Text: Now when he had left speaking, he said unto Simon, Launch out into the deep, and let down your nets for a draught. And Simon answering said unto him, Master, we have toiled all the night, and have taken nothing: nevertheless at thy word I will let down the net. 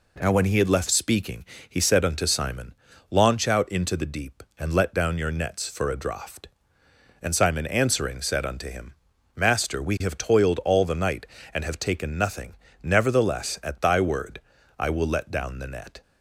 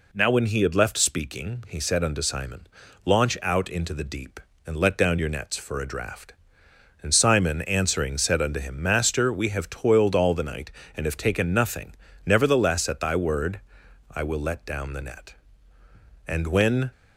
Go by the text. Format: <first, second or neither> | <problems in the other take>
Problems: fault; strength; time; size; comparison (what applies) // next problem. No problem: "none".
first | pauses between "word" and "I"; noticeable; at 13.6 s; 0.50 s long; slight in the first // goes on to say "And when"; noticeable; from 16.2 s on; 0.64 s long